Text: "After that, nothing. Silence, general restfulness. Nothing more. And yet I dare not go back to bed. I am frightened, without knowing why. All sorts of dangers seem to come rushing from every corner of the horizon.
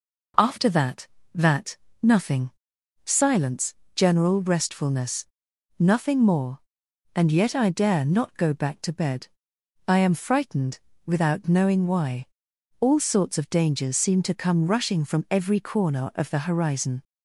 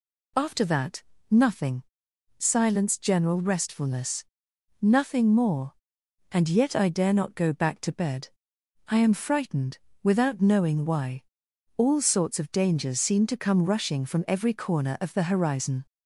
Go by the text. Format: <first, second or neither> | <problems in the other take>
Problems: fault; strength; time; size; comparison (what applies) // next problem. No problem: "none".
second | says "that" twice; at 1.3 s